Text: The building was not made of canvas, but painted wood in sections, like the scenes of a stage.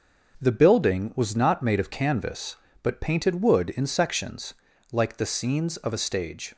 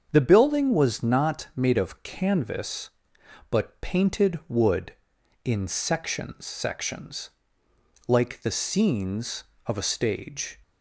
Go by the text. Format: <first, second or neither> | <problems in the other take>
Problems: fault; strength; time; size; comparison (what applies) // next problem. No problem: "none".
first | starts louder than the rest; until 1.1 s; 7 dB; noticeable in the first // says "sections" twice; at 6.4 s